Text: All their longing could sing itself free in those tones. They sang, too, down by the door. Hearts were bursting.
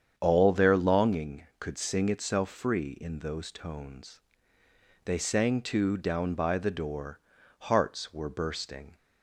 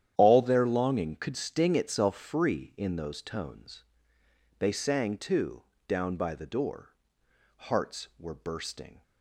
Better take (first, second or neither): first